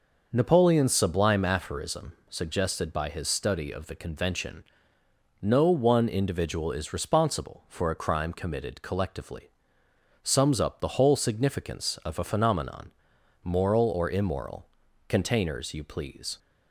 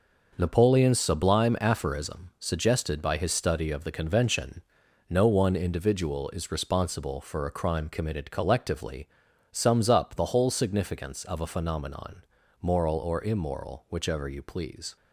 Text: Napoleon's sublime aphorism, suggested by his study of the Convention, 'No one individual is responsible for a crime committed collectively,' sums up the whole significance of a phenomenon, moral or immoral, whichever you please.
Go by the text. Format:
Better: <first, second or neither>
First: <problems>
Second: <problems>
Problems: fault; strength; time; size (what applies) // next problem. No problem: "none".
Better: second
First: says "containers" for "whichever"; at 15.0 s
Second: none